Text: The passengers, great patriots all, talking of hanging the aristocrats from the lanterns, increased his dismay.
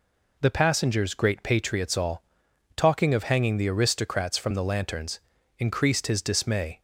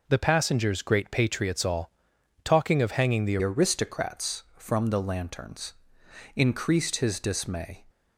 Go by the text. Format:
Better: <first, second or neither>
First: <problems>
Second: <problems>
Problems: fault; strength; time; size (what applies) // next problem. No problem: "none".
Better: first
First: none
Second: changes voice at "aristocrats"; from 3.4 s on; 4.4 s long